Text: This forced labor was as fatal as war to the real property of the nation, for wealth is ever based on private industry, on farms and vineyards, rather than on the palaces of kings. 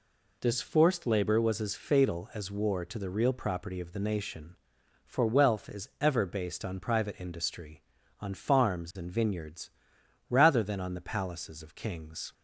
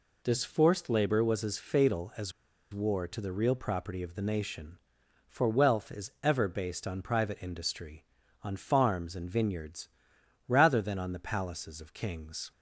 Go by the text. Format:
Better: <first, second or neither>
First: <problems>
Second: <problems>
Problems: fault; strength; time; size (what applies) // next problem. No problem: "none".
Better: first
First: none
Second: pauses between "as" and "war"; at 2.3 s; 0.41 s long